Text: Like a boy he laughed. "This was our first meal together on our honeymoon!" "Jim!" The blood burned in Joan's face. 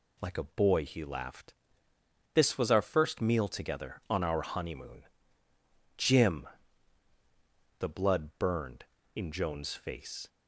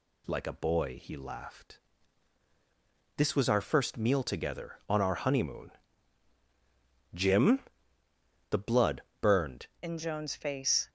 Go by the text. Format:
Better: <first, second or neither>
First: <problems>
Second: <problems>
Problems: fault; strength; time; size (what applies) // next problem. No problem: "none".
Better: first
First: none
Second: pauses between "blood" and "burned"; slight; at 9.0 s; 0.18 s long // changes voice at "in"; from 9.8 s on; 1.0 s long